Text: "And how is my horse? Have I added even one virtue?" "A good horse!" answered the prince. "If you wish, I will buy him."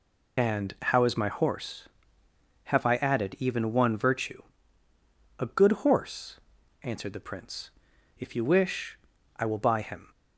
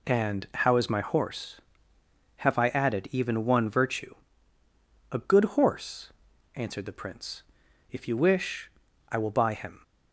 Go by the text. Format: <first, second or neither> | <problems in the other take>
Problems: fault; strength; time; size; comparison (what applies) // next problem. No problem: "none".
second | loses the start of "And"; at 0.3 s; 45 ms